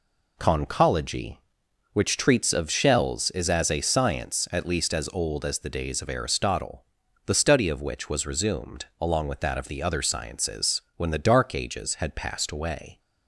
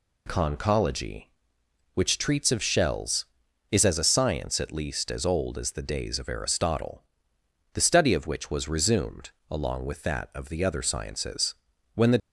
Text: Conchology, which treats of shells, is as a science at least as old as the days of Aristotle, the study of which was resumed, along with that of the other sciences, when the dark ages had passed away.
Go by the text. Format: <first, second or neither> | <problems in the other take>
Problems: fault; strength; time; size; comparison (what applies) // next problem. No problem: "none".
first | stops before "dark ages had passed away"; at 12.2 s